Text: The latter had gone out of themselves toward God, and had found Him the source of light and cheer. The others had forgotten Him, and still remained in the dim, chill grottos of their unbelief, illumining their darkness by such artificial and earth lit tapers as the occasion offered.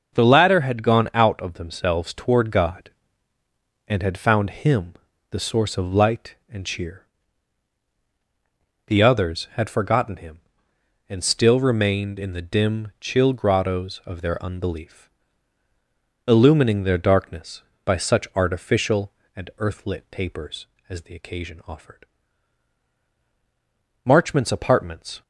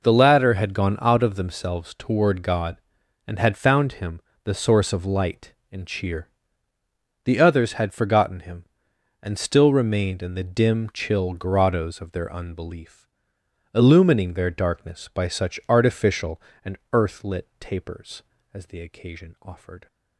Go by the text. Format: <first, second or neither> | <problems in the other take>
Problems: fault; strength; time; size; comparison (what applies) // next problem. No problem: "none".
second | pauses between "Him" and "the"; at 4.9 s; 0.38 s long; slight in the second // goes on to say "Marchmont's apartments"; noticeable; from 24.0 s on; 1.1 s long